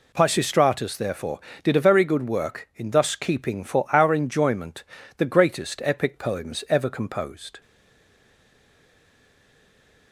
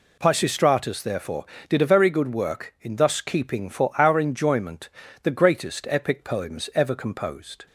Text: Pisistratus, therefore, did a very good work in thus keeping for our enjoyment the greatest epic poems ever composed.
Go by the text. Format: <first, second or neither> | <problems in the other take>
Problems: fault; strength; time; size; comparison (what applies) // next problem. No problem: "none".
second | pauses between "enjoyment" and "the"; slight; at 4.8 s; 0.36 s long; slight in the second // stays silent after the last word; from 7.6 s on; 2.5 s long